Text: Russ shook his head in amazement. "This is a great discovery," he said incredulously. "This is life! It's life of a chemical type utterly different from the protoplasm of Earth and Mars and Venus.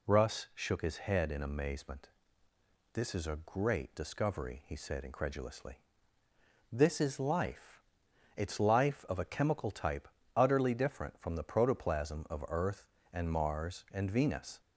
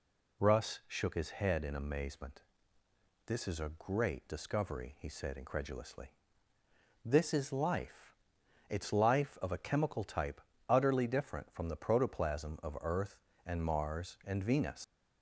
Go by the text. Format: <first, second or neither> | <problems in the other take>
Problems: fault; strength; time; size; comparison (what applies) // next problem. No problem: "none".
first | pauses between "type" and "utterly"; slight; at 10.3 s; 0.30 s long; slight in the first // leaves "Venus" unfinished; at 14.8 s; 90 ms